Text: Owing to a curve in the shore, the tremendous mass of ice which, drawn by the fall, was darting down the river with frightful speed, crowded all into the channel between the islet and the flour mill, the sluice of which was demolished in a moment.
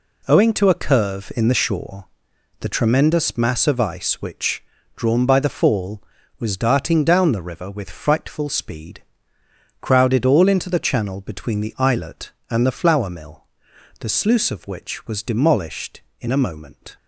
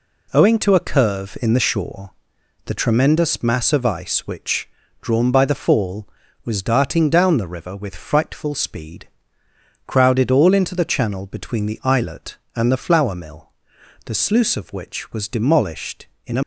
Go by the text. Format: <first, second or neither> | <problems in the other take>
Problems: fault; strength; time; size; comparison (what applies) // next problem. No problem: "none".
first | stops before "moment"; at 16.4 s